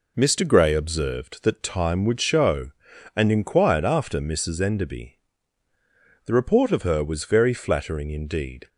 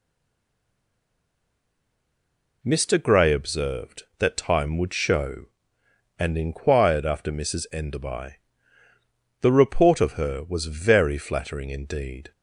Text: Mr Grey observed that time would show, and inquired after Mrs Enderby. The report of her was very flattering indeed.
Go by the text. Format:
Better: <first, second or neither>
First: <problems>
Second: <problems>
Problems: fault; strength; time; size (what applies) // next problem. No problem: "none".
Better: first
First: none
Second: stays silent before the first word; strong; until 2.6 s; 2.6 s long